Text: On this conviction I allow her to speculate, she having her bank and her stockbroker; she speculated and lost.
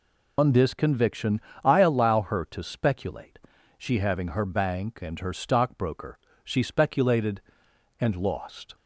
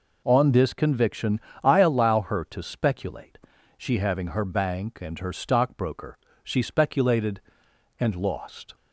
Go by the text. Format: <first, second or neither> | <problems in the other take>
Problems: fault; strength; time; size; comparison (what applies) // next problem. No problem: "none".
second | loses the start of "On"; at 0.3 s; 130 ms // pauses between "conviction" and "I"; slight; at 1.4 s; 0.22 s long; slight in the second